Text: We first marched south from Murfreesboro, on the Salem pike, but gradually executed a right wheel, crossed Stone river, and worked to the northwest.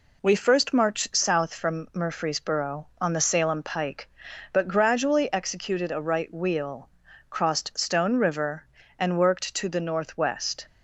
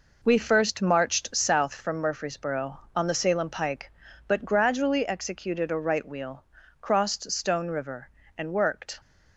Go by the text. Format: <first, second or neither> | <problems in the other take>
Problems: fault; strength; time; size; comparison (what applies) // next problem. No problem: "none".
first | stops before "to the northwest"; at 9.0 s